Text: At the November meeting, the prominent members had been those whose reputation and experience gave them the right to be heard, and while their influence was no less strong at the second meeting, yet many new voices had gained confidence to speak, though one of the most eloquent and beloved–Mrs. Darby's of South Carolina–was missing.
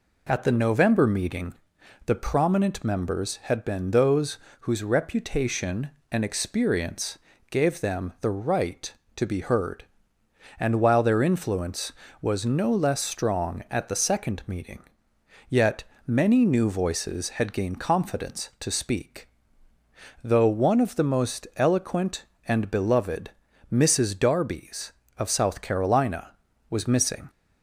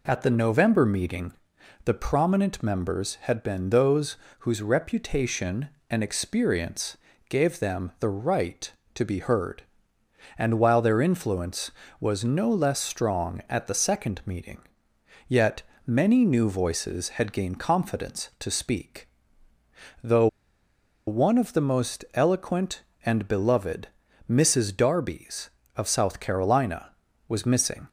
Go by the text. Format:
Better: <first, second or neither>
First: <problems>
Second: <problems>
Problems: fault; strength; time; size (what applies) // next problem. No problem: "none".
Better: first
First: pauses between "those" and "whose"; slight; at 4.3 s; 0.24 s long // pauses between "experience" and "gave"; slight; at 7.1 s; 0.32 s long // pauses between "yet" and "many"; slight; at 15.8 s; 0.25 s long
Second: pauses between "those" and "whose"; slight; at 4.1 s; 0.24 s long // pauses between "experience" and "gave"; slight; at 6.9 s; 0.32 s long // pauses between "yet" and "many"; slight; at 15.6 s; 0.26 s long // pauses between "though" and "one"; noticeable; at 20.2 s; 0.79 s long